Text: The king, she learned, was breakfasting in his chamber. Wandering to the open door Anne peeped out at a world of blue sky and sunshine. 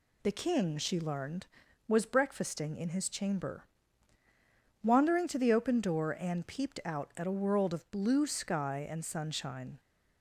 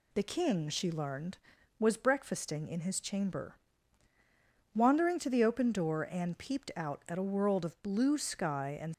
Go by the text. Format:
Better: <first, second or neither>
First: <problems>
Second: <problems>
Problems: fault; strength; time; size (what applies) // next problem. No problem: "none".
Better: first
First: none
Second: stops before "sunshine"; at 8.9 s